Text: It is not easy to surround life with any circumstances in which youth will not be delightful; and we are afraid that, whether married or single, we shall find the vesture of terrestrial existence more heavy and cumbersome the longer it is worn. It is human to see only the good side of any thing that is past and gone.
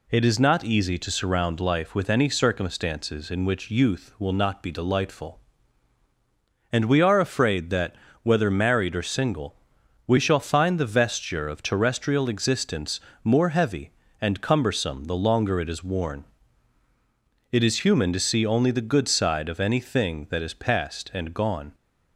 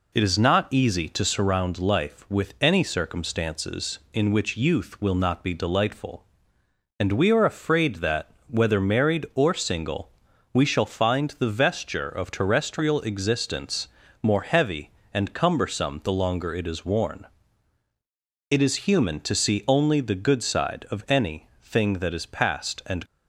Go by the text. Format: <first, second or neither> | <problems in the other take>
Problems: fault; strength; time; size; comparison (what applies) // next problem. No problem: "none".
first | pauses between "existence" and "more"; slight; at 13.8 s; 0.34 s long; slight in the first // pauses between "any" and "thing"; slight; at 21.4 s; 0.16 s long // stops before "gone"; at 23.0 s